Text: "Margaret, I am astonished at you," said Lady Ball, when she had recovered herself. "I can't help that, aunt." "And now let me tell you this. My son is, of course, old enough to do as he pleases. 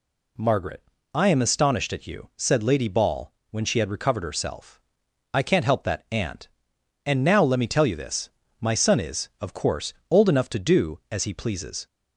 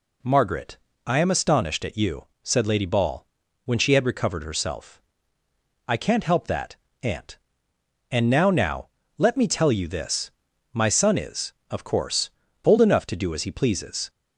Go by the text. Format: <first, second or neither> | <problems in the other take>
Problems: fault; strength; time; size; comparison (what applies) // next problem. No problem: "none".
first | says "now" twice; at 8.5 s